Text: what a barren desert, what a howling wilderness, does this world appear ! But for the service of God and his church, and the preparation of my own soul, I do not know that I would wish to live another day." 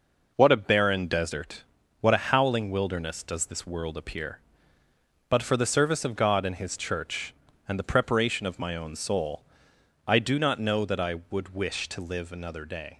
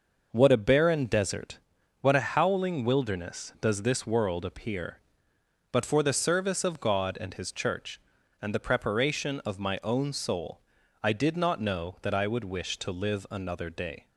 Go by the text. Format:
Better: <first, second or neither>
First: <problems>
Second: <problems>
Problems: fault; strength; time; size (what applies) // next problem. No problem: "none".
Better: first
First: none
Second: says "did" for "do"; at 11.1 s